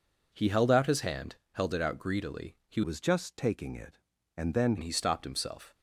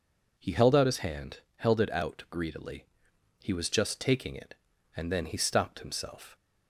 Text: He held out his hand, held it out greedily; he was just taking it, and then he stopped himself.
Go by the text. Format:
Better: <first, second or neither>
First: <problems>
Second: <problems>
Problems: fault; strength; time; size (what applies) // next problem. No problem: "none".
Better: second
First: changes voice from "was" to "then"; from 2.8 to 4.7 s; 1.9 s long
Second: none